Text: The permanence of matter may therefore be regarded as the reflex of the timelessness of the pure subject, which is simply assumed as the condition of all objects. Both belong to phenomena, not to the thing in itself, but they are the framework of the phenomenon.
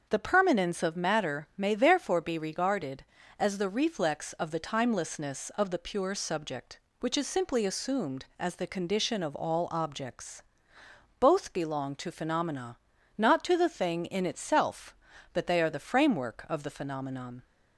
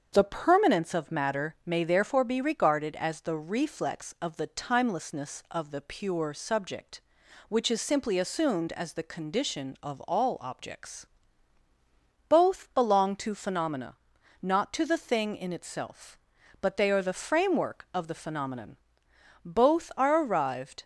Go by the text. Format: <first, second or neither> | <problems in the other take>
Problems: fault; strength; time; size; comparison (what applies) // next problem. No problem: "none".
first | starts louder than the rest; strong; until 1.1 s; 7 dB; also in the first // goes on to say "Both are arrived"; from 19.4 s on; 1.3 s long